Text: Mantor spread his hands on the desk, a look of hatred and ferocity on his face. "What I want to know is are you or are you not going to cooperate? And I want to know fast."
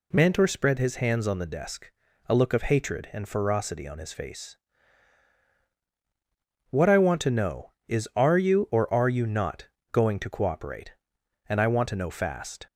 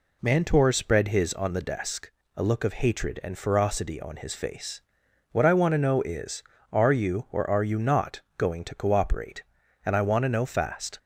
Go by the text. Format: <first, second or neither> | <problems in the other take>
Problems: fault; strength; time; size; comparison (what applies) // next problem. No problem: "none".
first | skips "hands"; at 1.3 s // pauses between "not" and "going"; slight; at 8.2 s; 0.18 s long; slight in the first